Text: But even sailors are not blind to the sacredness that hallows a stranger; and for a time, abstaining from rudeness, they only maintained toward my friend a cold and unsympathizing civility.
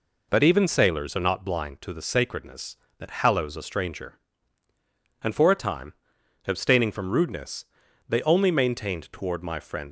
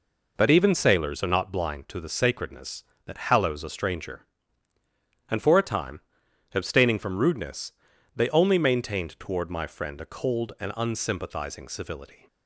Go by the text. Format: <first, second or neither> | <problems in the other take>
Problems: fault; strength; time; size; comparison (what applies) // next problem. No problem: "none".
second | stops before "a cold and unsympathizing civility"; at 9.8 s